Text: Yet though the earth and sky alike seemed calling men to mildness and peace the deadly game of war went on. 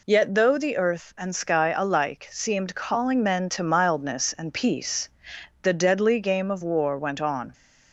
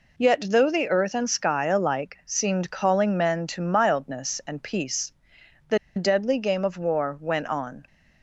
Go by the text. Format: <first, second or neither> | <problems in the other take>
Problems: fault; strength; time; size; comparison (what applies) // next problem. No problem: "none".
first | pauses between "peace" and "the"; noticeable; at 5.1 s; 0.56 s long; noticeable in the first // pauses between "the" and "deadly"; slight; at 5.7 s; 0.18 s long